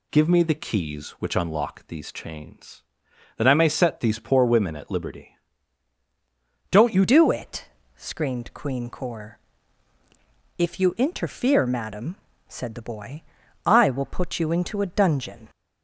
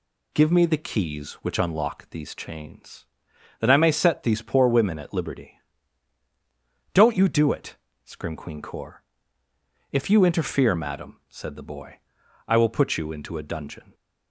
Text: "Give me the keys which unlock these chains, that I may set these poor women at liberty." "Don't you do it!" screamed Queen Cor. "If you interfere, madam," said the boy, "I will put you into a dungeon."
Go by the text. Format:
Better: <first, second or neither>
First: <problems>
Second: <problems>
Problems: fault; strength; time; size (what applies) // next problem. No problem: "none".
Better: second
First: changes voice at "do"; from 7.0 s on; 8.4 s long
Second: none